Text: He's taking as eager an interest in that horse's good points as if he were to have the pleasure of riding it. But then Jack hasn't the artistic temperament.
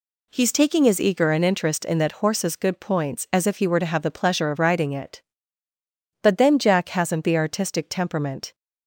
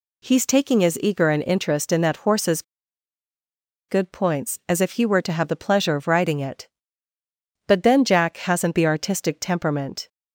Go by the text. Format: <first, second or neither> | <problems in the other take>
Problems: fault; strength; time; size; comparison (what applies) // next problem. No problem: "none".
first | pauses between "horse's" and "good"; strong; at 2.6 s; 1.2 s long